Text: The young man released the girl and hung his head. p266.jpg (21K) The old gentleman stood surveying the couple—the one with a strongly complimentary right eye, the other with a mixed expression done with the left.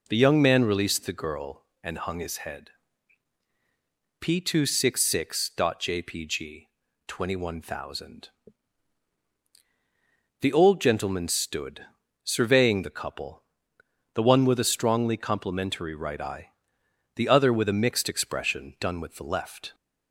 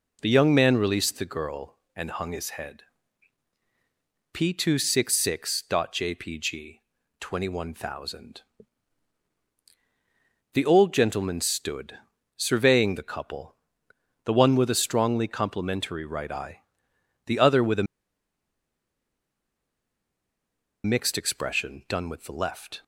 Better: first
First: pauses between "stood" and "surveying"; slight; at 11.8 s; 0.36 s long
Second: pauses between "stood" and "surveying"; slight; at 11.9 s; 0.36 s long // pauses between "a" and "mixed"; strong; at 17.8 s; 3.0 s long

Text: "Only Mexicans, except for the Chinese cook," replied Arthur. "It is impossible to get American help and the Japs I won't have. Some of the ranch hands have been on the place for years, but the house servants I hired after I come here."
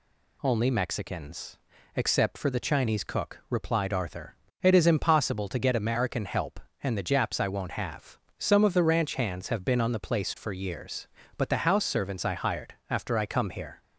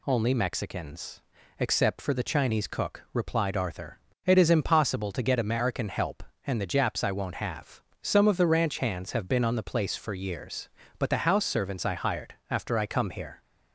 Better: neither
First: pauses between "hired" and "after"; slight; at 12.7 s; 0.16 s long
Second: pauses between "hired" and "after"; slight; at 12.3 s; 0.16 s long

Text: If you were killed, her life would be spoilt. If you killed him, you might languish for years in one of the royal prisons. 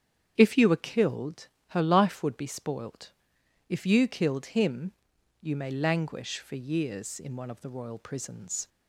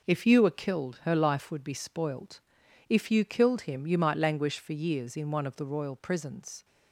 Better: second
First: starts louder than the rest; strong; until 1.3 s; 8.5 dB // says "may" for "might"; at 5.5 s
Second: none

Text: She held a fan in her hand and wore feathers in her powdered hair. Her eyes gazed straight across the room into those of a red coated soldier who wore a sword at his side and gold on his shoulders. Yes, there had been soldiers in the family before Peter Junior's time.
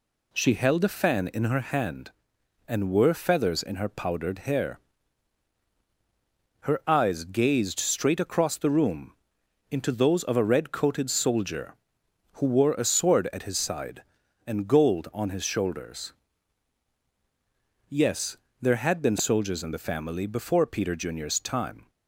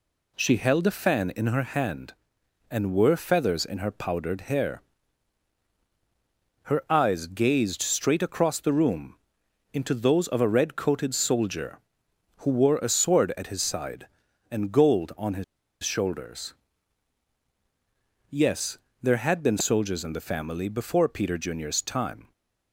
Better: first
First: pauses between "room" and "into"; noticeable; at 9.1 s; 0.56 s long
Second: pauses between "room" and "into"; noticeable; at 9.1 s; 0.56 s long // pauses between "his" and "shoulders"; at 15.4 s; 0.39 s long

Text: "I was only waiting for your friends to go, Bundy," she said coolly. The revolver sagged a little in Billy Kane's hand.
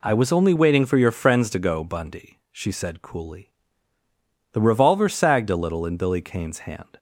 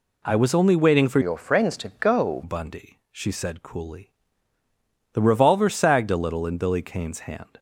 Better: first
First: none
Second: changes voice from "your" to "go"; from 1.2 to 2.4 s; 1.2 s long

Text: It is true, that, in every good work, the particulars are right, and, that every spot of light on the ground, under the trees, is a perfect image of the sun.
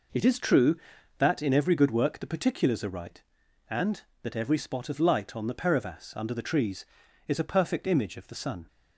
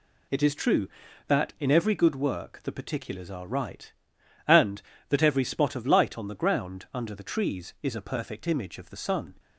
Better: second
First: says "perivas" for "ground"; at 5.5 s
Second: none

